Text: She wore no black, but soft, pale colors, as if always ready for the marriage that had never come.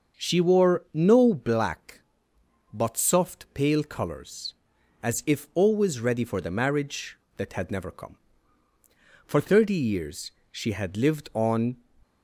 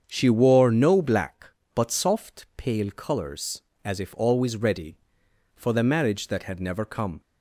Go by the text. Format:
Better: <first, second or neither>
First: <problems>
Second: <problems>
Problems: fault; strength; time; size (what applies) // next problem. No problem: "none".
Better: second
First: starts louder than the rest; until 1.2 s; 6 dB // goes on to say "For thirty years she had lived on"; strong; from 9.2 s on; 2.5 s long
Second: starts louder than the rest; strong; until 1.0 s; 7 dB